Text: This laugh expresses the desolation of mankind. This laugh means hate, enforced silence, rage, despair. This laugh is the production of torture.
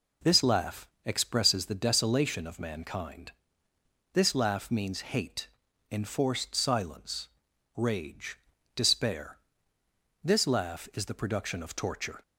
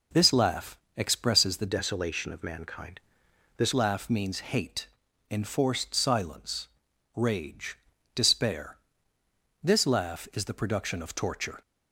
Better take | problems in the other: first | pauses between "laugh" and "expresses"; slight; at 0.7 s; 0.18 s long; slight in the first // changes voice from "desolation" to "This"; from 1.6 to 3.7 s; 2.1 s long

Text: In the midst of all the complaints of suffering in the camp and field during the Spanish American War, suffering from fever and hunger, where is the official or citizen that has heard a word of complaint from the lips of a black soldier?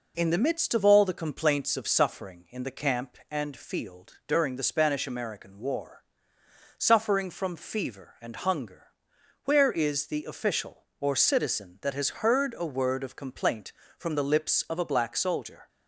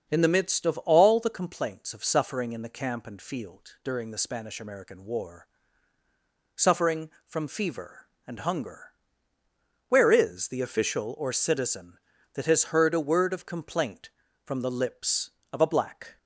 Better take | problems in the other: first | starts louder than the rest; until 1.1 s; 7 dB // stops before "soldier"; at 16.1 s

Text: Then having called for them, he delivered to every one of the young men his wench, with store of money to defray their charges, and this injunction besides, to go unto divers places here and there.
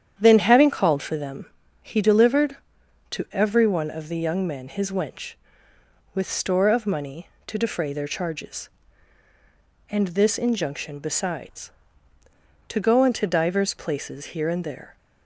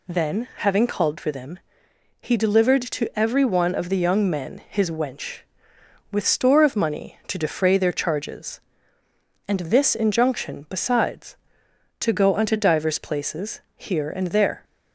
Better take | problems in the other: second | starts louder than the rest; strong; until 1.2 s; 9 dB

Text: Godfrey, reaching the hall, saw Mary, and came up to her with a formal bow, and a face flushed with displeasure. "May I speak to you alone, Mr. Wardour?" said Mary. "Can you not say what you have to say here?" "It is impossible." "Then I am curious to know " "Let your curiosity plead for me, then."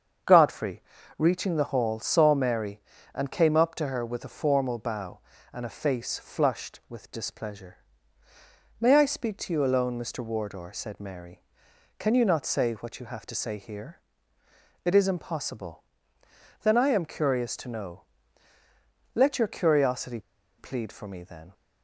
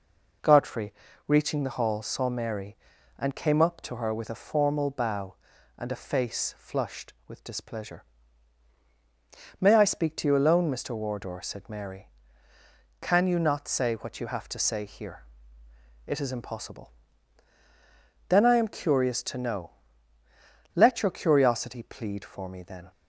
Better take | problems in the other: second | starts louder than the rest; until 1.6 s; 7 dB // pauses between "curiosity" and "plead"; at 20.1 s; 0.39 s long

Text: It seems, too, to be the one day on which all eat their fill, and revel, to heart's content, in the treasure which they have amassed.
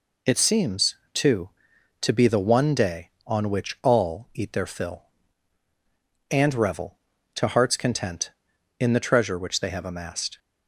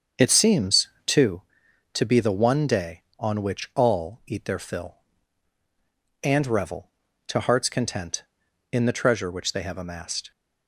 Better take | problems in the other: first | starts louder than the rest; until 1.4 s; 7 dB

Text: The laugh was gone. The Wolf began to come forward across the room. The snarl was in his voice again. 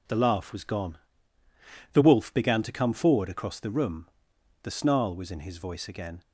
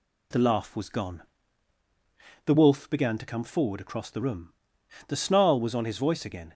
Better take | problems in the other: first | says "on" for "in"; at 5.7 s

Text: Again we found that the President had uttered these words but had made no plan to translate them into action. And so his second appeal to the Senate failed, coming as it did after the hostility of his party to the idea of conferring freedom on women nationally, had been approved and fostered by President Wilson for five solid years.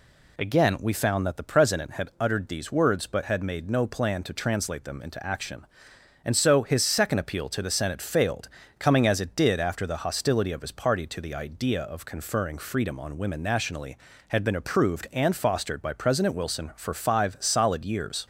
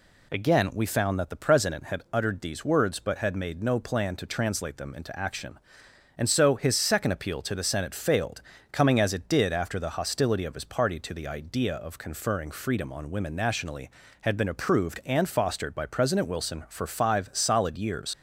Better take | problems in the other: first | leaves "years" unfinished; at 18.1 s; 50 ms

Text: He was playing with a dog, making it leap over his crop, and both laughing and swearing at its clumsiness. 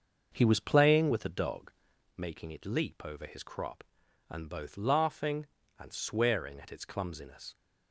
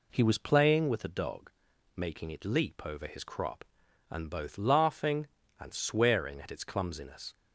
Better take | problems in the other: second | starts louder than the rest; until 2.1 s; 6 dB

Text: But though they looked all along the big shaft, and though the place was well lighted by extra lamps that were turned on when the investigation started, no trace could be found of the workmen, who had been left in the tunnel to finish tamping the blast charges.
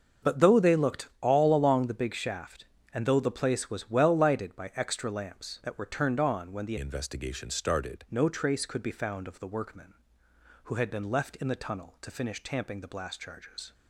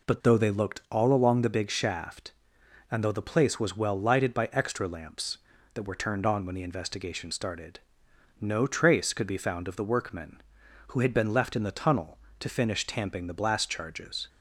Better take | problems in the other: second | starts louder than the rest; until 1.3 s; 6 dB // changes voice from "investigation" to "started"; from 6.7 to 8.0 s; 1.3 s long

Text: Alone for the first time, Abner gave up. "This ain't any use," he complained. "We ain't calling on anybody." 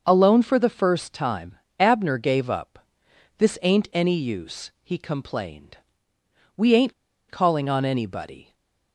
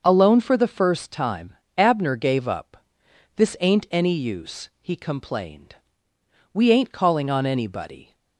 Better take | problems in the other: second | starts louder than the rest; until 1.0 s; 6 dB; also in the second // pauses between "ain't" and "calling"; at 6.9 s; 0.37 s long // stays silent after the last word; slight; from 8.4 s on; 0.5 s long

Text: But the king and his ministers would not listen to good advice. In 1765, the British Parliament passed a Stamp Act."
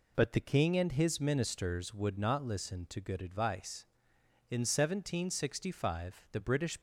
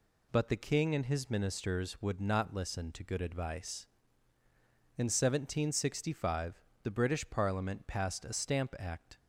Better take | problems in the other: second | stops before "Parliament passed a Stamp Act"; at 6.7 s

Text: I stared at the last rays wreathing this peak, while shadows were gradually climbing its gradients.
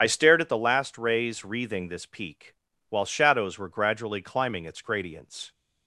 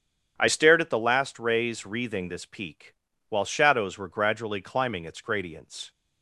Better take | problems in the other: second | loses the start of "I"; at 0.0 s; 45 ms // starts louder than the rest; strong; until 1.0 s; 8.5 dB; strong in the second

